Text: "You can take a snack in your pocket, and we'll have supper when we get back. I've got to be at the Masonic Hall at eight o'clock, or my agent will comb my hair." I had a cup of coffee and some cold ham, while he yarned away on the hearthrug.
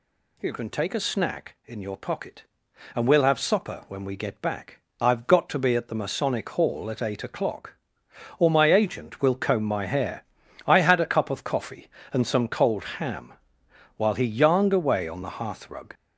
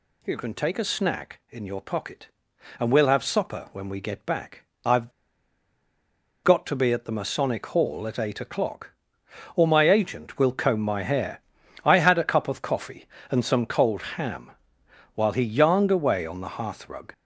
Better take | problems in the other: first | pauses between "I've" and "got"; strong; at 5.0 s; 1.3 s long // pauses between "cold" and "ham"; slight; at 14.0 s; 0.16 s long; slight in the first

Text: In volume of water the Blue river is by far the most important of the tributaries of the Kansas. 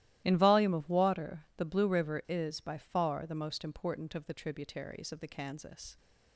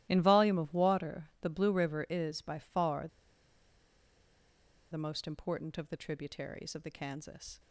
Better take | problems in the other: first | starts louder than the rest; strong; until 1.1 s; 15 dB; strong in the first // pauses between "far" and "the"; strong; at 3.0 s; 1.8 s long

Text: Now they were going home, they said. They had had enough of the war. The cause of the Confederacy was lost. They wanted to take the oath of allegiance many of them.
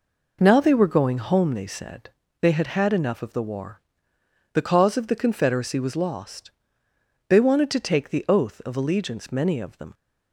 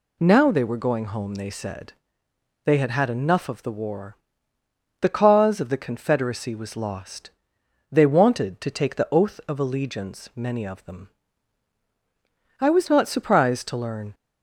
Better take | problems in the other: first | goes on to say "I was not surprised to learn"; from 12.5 s on; 1.5 s long

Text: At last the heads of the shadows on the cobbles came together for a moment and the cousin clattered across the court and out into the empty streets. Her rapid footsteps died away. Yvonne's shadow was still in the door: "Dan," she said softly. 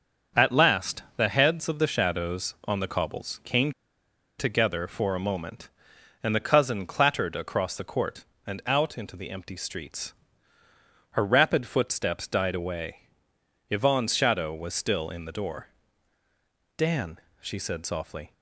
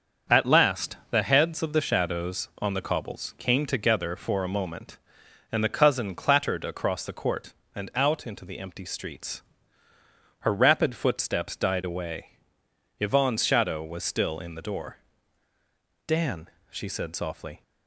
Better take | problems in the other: second | starts louder than the rest; until 1.4 s; 6.5 dB; also in the second // pauses between "came" and "together"; noticeable; at 3.7 s; 0.67 s long

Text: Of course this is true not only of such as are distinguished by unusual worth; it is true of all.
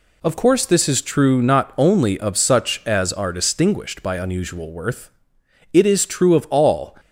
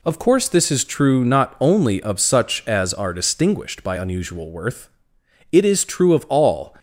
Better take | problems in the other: neither | none

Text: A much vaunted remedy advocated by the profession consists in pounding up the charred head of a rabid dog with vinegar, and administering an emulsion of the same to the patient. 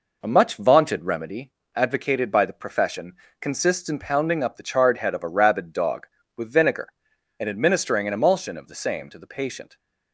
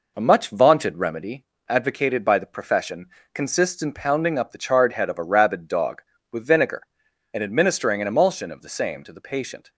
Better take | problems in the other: neither | pauses between "remedy" and "advocated"; slight; the same in both // pauses between "profession" and "consists"; slight; the same in both

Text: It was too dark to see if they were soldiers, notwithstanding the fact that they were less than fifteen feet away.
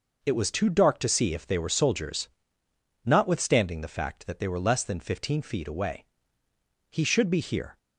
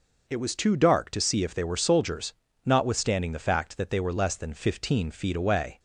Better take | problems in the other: second | goes on to say "He should be here"; noticeable; from 6.8 s on; 0.88 s long

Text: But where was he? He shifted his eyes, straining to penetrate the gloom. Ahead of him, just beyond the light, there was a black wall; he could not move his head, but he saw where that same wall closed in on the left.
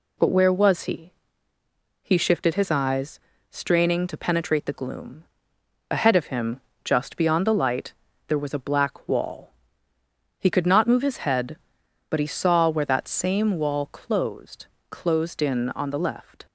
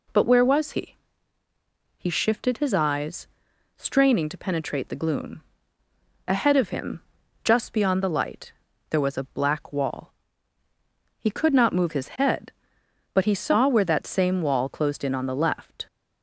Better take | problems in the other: second | says "closed" twice; at 14.8 s

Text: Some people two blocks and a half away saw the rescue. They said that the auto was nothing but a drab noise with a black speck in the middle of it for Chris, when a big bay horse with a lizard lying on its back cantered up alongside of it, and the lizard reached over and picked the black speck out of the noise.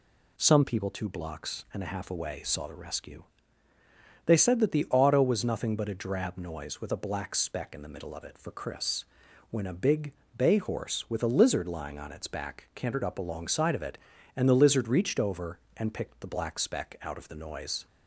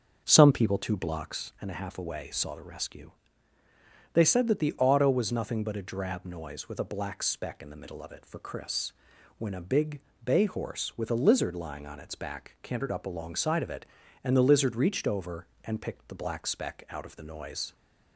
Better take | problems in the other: first | starts louder than the rest; until 1.4 s; 6.5 dB // pauses between "big" and "bay"; slight; at 9.9 s; 0.24 s long; slight in the first

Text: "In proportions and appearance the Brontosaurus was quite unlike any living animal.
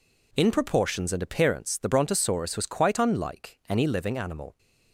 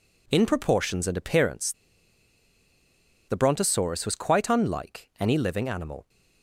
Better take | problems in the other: first | pauses between "appearance" and "the"; strong; at 1.7 s; 1.5 s long

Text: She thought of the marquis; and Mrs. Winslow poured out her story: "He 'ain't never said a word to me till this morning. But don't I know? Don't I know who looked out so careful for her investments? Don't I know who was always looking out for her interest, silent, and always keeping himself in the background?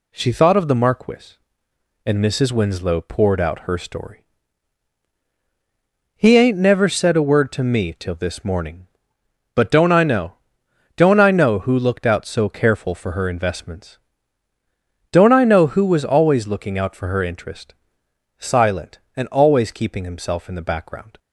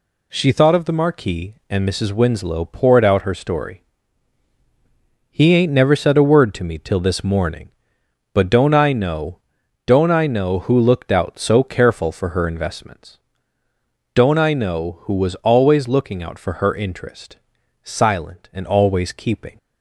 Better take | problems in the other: first | stops before "himself in the background"; at 19.5 s

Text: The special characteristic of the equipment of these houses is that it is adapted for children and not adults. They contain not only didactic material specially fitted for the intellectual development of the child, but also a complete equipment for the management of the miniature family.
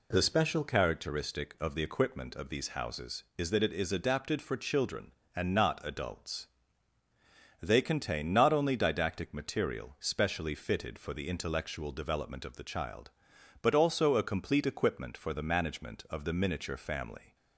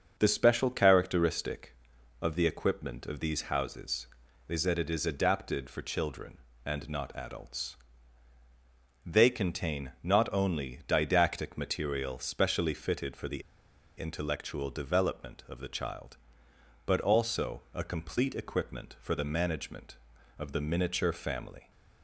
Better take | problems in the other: first | starts louder than the rest; until 1.2 s; 6.5 dB // pauses between "the" and "intellectual"; noticeable; at 13.4 s; 0.56 s long

